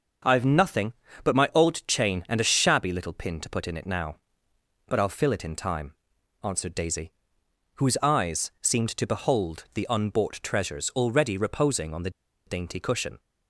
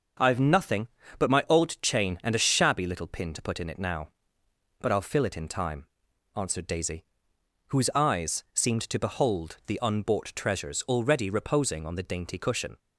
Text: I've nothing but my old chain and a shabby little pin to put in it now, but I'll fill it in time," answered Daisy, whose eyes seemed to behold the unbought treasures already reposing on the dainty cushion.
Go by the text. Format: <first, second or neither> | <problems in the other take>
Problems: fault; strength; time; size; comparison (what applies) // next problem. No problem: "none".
second | starts louder than the rest; until 1.6 s; 6.5 dB; also in the second // pauses between "the" and "dainty"; at 12.0 s; 0.37 s long